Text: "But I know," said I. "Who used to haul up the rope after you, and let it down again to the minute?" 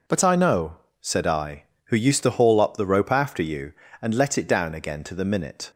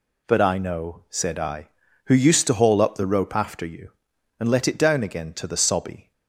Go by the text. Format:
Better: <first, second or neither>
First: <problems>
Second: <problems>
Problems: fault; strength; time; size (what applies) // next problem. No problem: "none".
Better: first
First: none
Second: says "sobby" for "minute"; at 5.5 s